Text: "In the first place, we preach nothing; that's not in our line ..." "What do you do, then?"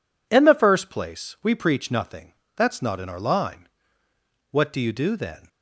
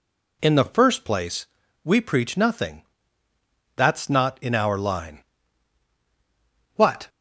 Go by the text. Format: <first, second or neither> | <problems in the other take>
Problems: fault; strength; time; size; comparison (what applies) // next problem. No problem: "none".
first | stops before "do you do then"; at 7.0 s